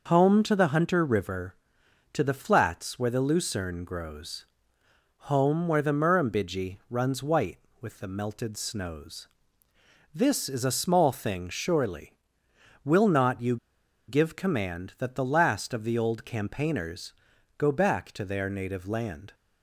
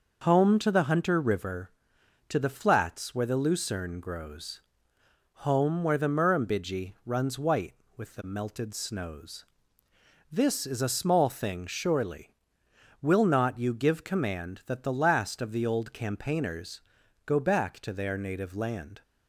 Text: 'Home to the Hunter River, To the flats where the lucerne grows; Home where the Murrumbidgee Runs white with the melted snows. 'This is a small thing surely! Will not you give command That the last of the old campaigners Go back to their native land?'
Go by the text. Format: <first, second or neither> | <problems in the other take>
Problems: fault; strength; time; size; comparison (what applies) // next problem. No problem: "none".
second | pauses between "you" and "give"; noticeable; at 13.5 s; 0.51 s long // pauses between "campaigners" and "Go"; noticeable; at 17.1 s; 0.46 s long; noticeable in the second